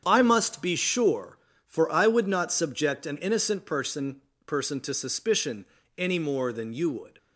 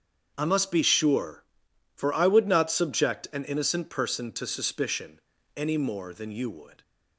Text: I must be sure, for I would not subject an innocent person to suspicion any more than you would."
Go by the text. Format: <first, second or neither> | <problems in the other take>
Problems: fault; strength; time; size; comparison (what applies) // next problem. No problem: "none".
second | starts louder than the rest; strong; until 1.0 s; 8 dB; strong in the second // says "person" twice; at 4.4 s // pauses between "suspicion" and "any"; slight; at 5.6 s; 0.32 s long; slight in the second